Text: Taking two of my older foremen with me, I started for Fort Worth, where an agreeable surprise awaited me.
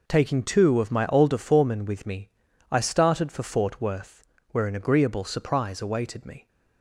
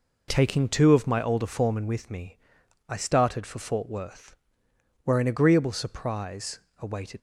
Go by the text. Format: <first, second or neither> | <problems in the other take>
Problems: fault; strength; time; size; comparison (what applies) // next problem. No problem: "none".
first | pauses between "surprise" and "awaited"; slight; at 6.5 s; 0.20 s long // stops before "me"; at 7.1 s